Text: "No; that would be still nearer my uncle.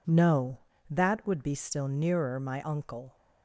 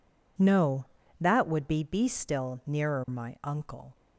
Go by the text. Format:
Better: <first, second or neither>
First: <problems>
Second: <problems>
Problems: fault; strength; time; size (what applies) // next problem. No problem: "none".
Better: first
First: none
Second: says "be" twice; at 1.8 s